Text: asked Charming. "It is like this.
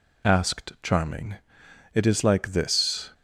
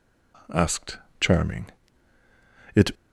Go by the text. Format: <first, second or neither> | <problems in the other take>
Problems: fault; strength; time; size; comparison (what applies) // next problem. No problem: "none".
first | pauses between "asked" and "Charming"; slight; at 0.9 s; 0.22 s long // stops before "is like this"; at 2.9 s